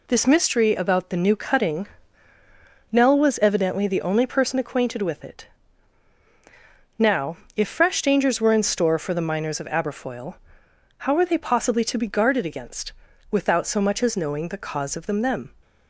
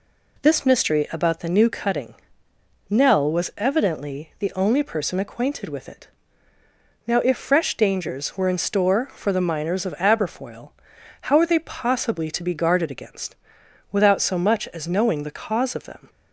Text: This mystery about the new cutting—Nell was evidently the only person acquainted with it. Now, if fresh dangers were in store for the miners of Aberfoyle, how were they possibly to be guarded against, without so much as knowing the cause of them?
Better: second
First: says "them" twice; at 15.2 s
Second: none

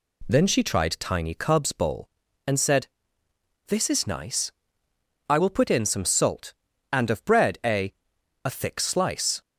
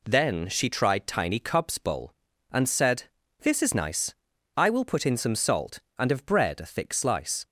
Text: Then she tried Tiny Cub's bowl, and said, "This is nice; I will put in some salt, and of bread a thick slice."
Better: second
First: says "a" twice; at 8.4 s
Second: none

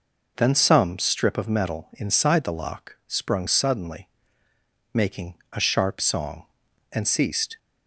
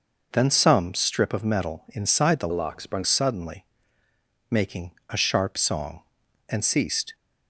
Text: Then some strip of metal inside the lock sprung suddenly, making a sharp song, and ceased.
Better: first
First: pauses between "making" and "a"; slight; at 5.3 s; 0.16 s long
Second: changes voice from "lock" to "sprung"; from 2.5 to 3.0 s; 0.5 s long // pauses between "making" and "a"; slight; at 4.9 s; 0.16 s long

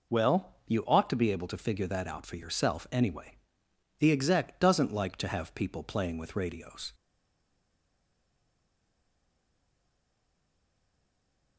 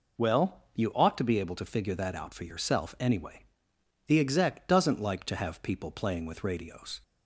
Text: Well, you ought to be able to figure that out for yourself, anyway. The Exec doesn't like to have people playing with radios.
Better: second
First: stays silent after the last word; strong; from 6.9 s on; 4.6 s long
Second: none

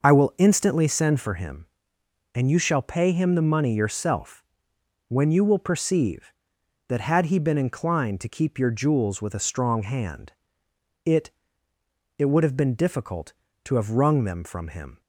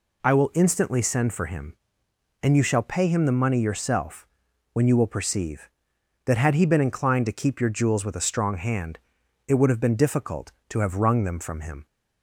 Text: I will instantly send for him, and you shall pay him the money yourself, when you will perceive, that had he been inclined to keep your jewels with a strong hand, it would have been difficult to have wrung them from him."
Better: second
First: says "it" twice; at 12.1 s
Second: none

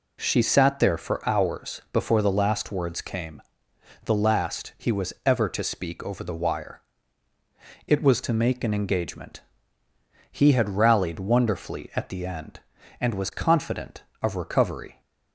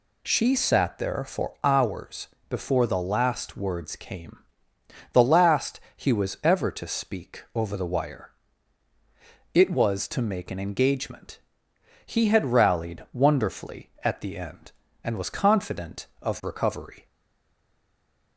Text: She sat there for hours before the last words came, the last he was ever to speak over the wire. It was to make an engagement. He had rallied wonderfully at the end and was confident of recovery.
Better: first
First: none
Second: pauses between "hours" and "before"; slight; at 2.2 s; 0.22 s long // pauses between "last" and "he"; slight; at 5.7 s; 0.18 s long // stays silent after the last word; noticeable; from 17.0 s on; 1.3 s long

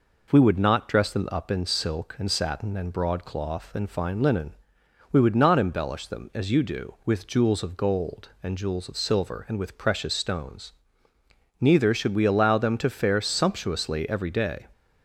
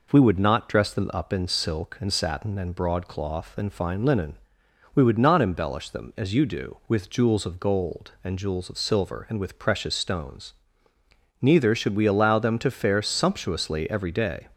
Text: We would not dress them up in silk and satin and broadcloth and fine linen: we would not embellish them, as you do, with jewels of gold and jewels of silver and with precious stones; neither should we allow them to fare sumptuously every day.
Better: neither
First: none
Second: none

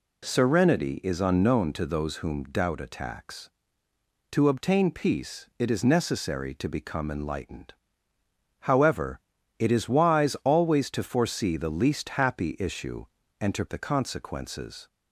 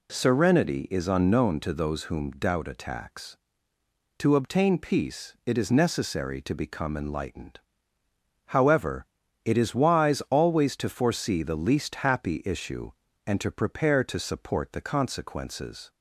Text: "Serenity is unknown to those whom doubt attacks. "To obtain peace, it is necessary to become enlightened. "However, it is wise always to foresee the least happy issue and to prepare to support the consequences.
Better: second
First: skips "prepare to support"; at 13.6 s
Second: none

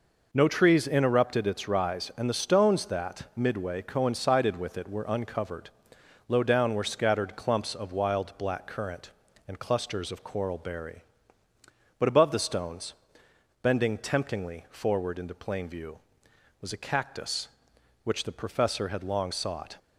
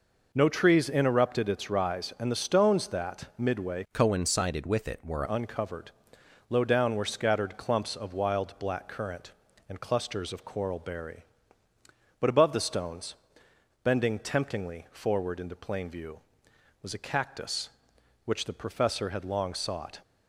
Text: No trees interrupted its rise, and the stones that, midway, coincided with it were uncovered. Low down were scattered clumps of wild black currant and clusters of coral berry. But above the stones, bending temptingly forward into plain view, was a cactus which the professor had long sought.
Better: first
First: none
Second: changes voice from "coincided" to "were"; from 3.9 to 5.2 s; 1.3 s long

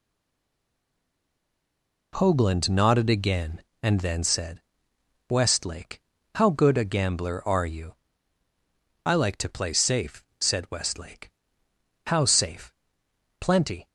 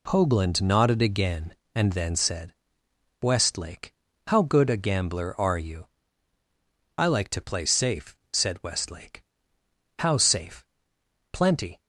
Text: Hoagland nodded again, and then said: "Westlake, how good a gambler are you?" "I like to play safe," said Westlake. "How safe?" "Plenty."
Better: second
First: stays silent before the first word; until 2.1 s; 2.1 s long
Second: none

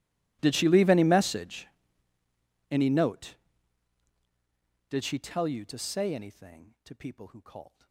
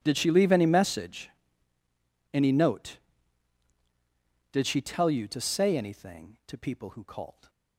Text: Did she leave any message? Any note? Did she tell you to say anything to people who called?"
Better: second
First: gets quieter; strong; throughout; 28.5 dB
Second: none

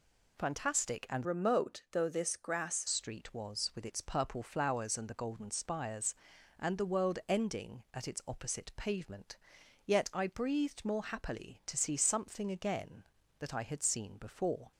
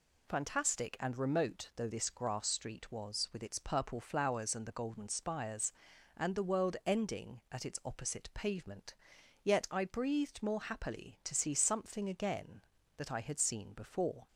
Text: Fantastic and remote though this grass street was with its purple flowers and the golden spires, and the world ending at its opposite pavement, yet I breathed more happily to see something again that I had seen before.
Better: second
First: changes voice from "remote" to "grass"; from 1.2 to 2.8 s; 1.6 s long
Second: none

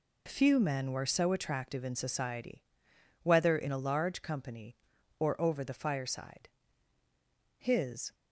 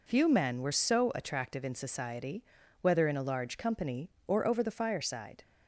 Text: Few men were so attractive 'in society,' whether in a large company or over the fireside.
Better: second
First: goes on to say "His"; from 7.5 s on; 0.56 s long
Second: none

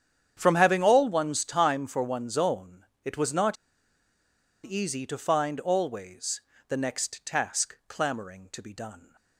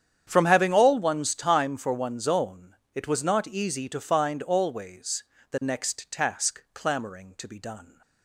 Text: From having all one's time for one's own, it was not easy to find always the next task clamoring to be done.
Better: second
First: starts louder than the rest; strong; until 1.3 s; 9 dB // pauses between "not" and "easy"; at 3.5 s; 1.0 s long // pauses between "always" and "the"; slight; at 6.4 s; 0.28 s long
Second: starts louder than the rest; strong; until 1.2 s; 9 dB // pauses between "always" and "the"; slight; at 5.2 s; 0.28 s long

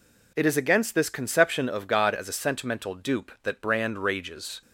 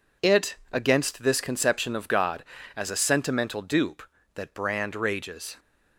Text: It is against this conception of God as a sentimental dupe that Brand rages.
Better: first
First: none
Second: skips "is"; at 0.6 s

